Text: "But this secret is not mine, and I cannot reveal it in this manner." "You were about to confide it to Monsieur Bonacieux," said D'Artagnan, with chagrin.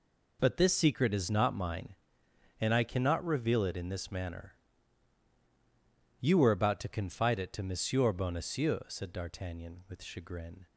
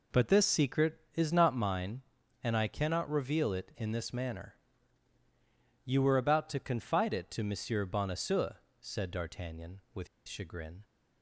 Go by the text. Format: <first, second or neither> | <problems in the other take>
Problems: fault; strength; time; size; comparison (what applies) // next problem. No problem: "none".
first | pauses between "with" and "chagrin"; slight; at 10.0 s; 0.20 s long